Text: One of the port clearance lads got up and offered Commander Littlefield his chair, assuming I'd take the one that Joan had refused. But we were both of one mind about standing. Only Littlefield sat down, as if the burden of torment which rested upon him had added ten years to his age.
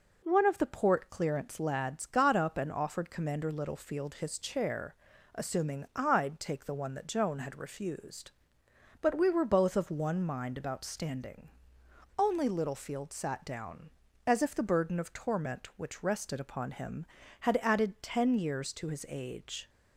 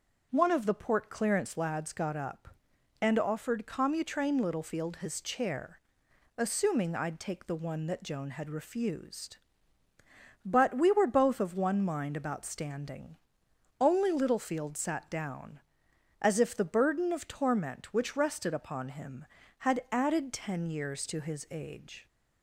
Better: first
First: none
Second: starts louder than the rest; until 1.3 s; 6.5 dB // says "Commutrain" for "Commander"; at 3.6 s

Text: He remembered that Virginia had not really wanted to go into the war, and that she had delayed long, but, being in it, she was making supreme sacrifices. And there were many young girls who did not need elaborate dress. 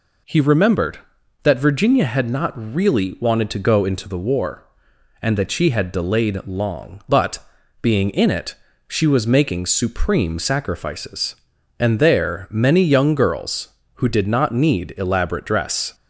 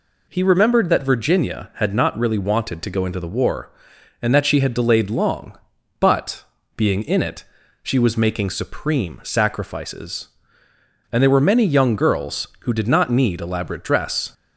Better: second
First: skips "were"; at 12.4 s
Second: none

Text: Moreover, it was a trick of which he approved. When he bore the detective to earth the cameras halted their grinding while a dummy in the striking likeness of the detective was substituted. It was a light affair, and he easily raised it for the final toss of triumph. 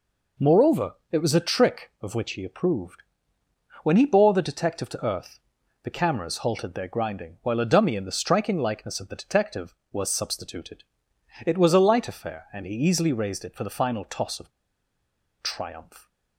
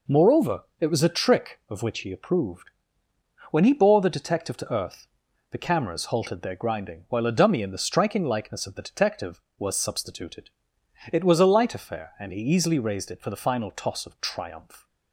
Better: second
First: pauses between "earth" and "the"; noticeable; at 5.3 s; 0.46 s long // pauses between "of" and "triumph"; noticeable; at 14.5 s; 0.91 s long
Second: pauses between "earth" and "the"; noticeable; at 5.0 s; 0.46 s long

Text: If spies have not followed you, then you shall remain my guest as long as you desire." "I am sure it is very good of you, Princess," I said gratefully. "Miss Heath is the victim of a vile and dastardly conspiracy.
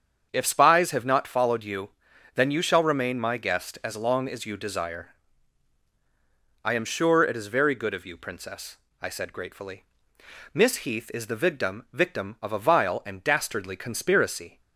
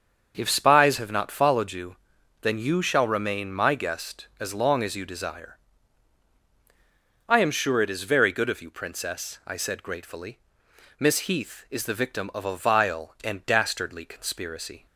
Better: second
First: starts louder than the rest; strong; until 1.3 s; 7.5 dB // says "victim" twice; at 11.9 s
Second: starts louder than the rest; until 1.3 s; 6.5 dB

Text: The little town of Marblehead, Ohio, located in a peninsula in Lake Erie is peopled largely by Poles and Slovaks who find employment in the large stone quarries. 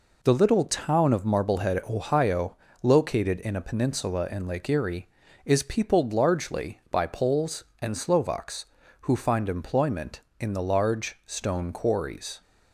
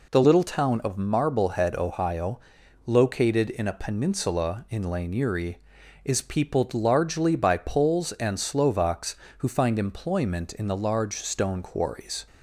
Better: first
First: none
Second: says "Lane" for "Lake"; at 4.8 s

